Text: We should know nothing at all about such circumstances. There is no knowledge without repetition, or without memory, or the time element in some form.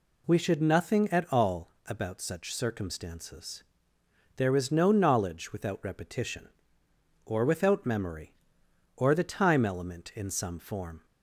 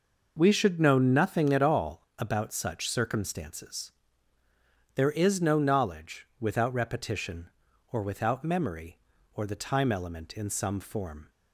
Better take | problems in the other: second | skips "know"; at 0.6 s // pauses between "all" and "about"; slight; at 1.6 s; 0.18 s long

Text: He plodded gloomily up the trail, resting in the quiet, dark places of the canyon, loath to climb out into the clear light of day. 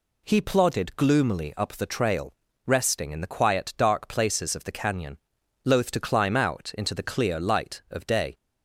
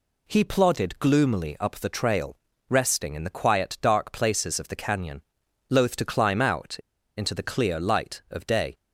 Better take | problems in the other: first | pauses between "out" and "into"; at 6.7 s; 0.41 s long

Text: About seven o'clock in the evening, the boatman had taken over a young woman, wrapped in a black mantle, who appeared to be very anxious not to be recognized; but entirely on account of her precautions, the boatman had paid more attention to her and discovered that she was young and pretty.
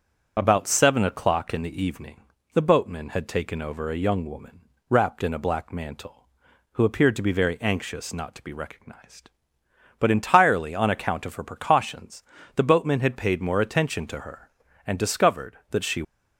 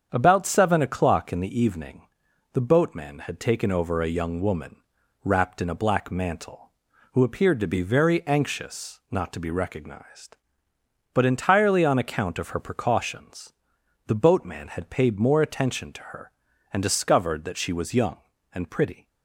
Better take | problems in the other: second | starts louder than the rest; until 1.3 s; 7 dB; strong in the second // stops before "was young and pretty"; at 16.0 s

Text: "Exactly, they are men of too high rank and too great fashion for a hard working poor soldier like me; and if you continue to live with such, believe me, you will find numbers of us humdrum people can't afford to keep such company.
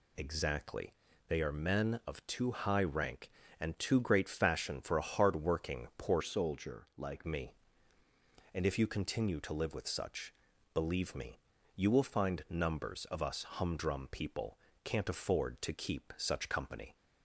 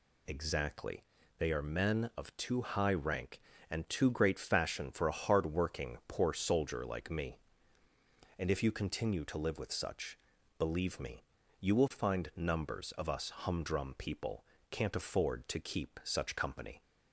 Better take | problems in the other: second | changes voice from "soldier" to "like"; from 6.2 to 7.2 s; 1.0 s long // pauses between "people" and "can't"; slight; at 14.5 s; 0.26 s long; slight in the second

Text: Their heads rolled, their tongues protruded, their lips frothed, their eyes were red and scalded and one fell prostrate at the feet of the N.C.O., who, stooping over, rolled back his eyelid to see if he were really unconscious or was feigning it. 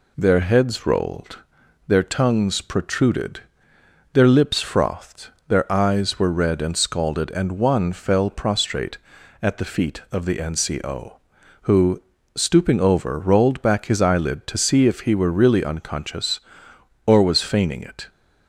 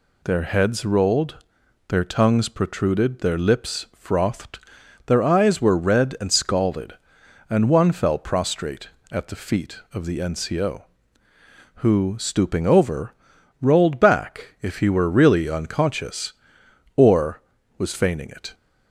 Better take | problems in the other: first | skips "his eyelid to see"; at 14.5 s

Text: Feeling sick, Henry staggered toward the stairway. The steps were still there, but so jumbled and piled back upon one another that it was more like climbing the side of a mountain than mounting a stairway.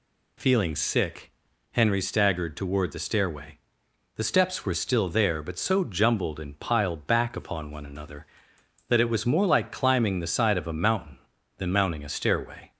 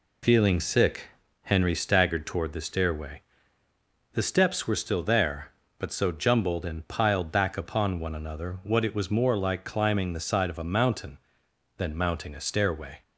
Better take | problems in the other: first | says "what" for "that"; at 8.6 s

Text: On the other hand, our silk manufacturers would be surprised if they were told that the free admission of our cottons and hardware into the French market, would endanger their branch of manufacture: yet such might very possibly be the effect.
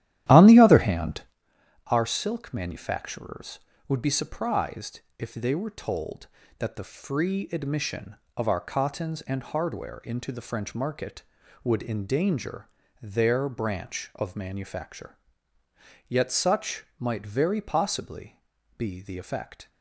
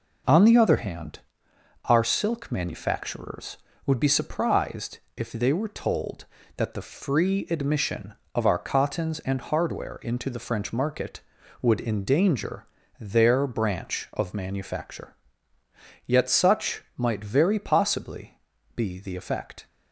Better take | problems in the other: second | starts louder than the rest; strong; until 1.4 s; 12.5 dB // pauses between "surprised" and "if"; slight; at 4.9 s; 0.18 s long; slight in the second // pauses between "endanger" and "their"; slight; at 12.6 s; 0.34 s long; slight in the second // pauses between "such" and "might"; slight; at 16.8 s; 0.16 s long; slight in the second // pauses between "possibly" and "be"; at 18.3 s; 0.38 s long; also in the second

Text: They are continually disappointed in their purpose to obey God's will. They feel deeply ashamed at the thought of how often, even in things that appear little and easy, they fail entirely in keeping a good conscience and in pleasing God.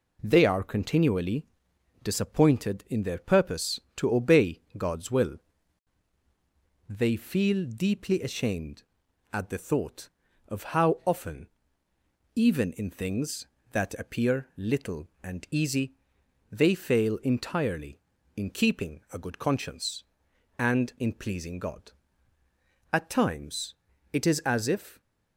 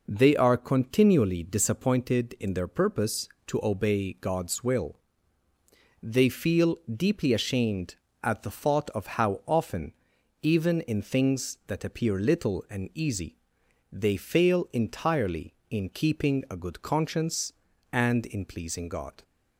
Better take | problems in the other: second | pauses between "continually" and "disappointed"; noticeable; at 1.4 s; 0.56 s long // pauses between "obey" and "God's"; slight; at 4.6 s; 0.16 s long // goes on to say "At times it is as if"; strong; from 22.9 s on; 2.0 s long

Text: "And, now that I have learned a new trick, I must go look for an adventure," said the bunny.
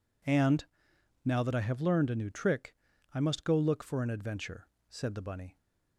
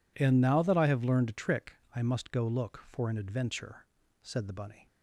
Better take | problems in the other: first | skips "new"; at 1.3 s

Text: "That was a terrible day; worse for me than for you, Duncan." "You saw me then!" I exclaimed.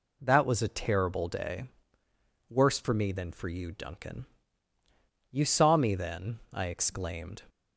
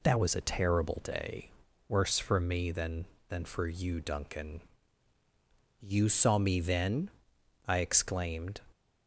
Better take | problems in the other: first | says "than" twice; at 3.2 s

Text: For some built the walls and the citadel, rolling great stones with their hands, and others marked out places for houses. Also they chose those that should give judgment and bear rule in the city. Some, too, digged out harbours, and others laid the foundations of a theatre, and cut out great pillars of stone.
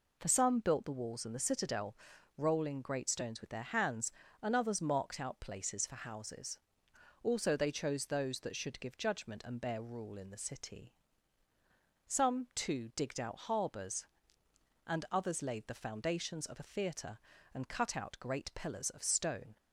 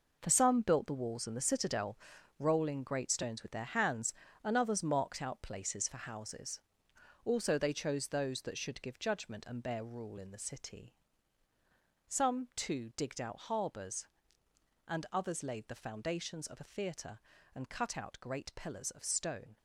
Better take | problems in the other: first | gets quieter; strong; throughout; 10 dB

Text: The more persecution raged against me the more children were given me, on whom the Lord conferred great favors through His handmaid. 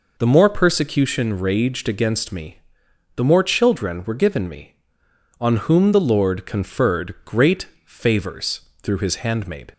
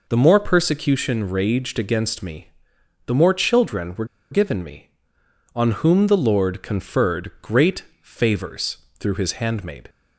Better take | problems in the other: first | pauses between "me" and "the"; noticeable; at 2.4 s; 0.56 s long; noticeable in the first // pauses between "were" and "given"; slight; at 4.0 s; 0.26 s long // pauses between "great" and "favors"; slight; at 7.8 s; 0.18 s long; slight in the first // pauses between "favors" and "through"; slight; at 8.7 s; 0.24 s long; slight in the first

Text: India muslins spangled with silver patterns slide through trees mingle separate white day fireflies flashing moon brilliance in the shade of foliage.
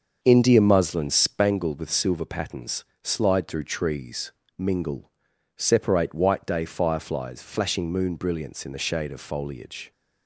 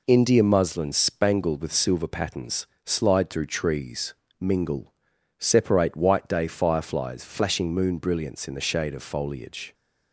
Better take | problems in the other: second | starts louder than the rest; until 1.6 s; 6.5 dB // pauses between "patterns" and "slide"; slight; at 2.8 s; 0.18 s long; slight in the second // pauses between "trees" and "mingle"; slight; at 4.3 s; 0.24 s long; slight in the second // pauses between "mingle" and "separate"; noticeable; at 5.0 s; 0.48 s long; noticeable in the second

